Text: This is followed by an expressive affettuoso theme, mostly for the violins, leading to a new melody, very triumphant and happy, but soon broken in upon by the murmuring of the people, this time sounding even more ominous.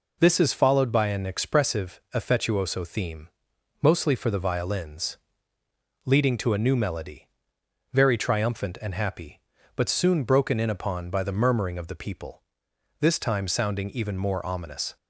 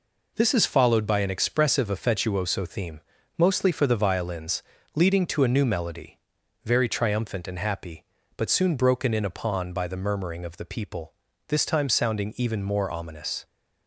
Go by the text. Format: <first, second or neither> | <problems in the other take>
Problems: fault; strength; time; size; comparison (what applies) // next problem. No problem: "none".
neither | none